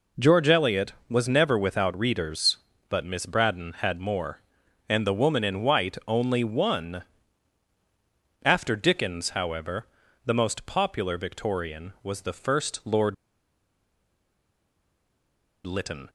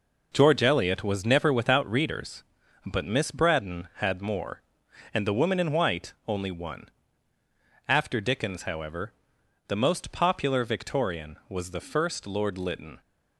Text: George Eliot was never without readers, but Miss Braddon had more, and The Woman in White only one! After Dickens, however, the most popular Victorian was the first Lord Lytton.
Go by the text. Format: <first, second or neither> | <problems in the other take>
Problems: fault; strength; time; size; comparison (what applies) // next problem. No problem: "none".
second | pauses between "Lord" and "Lytton"; strong; at 13.1 s; 2.5 s long